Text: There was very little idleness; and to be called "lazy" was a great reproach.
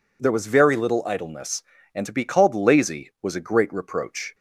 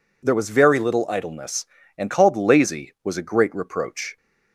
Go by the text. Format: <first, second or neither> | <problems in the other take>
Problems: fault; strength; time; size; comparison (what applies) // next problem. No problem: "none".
first | skips "to be"; at 2.0 s